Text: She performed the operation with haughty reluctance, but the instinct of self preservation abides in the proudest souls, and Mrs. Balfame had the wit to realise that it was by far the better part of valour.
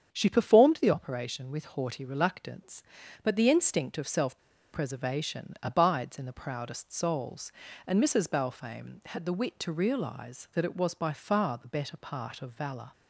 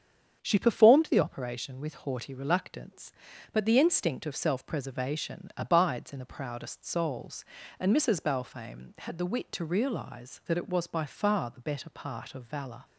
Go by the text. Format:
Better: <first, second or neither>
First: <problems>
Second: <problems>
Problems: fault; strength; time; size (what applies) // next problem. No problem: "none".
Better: second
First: starts louder than the rest; strong; until 1.1 s; 8 dB // pauses between "self" and "preservation"; at 4.3 s; 0.36 s long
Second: starts louder than the rest; strong; until 1.4 s; 8 dB